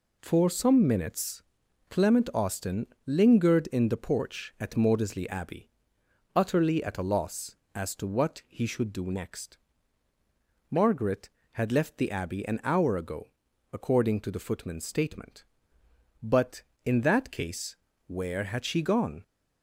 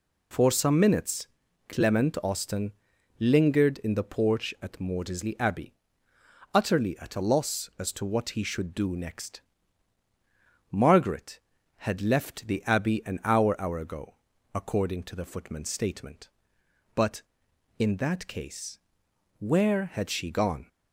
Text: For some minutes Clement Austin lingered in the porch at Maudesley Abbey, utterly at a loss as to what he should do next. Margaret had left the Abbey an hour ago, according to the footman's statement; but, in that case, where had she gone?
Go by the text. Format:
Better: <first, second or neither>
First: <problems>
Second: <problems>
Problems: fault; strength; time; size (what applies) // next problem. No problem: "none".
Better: first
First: pauses between "minutes" and "Clement"; noticeable; at 1.4 s; 0.48 s long // pauses between "Austin" and "lingered"; slight; at 2.8 s; 0.20 s long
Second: pauses between "minutes" and "Clement"; at 1.2 s; 0.42 s long // pauses between "Austin" and "lingered"; noticeable; at 2.7 s; 0.48 s long // says "hour" twice; at 13.5 s